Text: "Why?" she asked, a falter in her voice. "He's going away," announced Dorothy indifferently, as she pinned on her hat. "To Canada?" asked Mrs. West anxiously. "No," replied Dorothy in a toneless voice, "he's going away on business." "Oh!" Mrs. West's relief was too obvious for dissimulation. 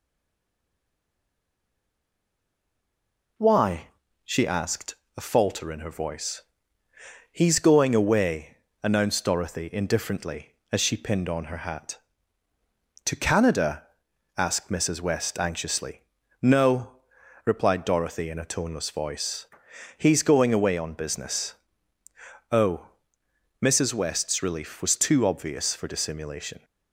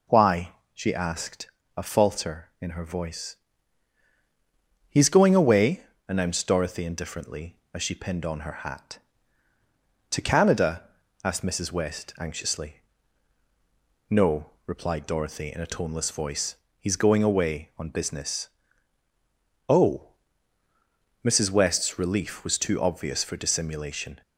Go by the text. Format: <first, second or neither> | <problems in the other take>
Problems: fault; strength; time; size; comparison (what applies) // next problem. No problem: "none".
second | stays silent before the first word; strong; until 3.3 s; 3.3 s long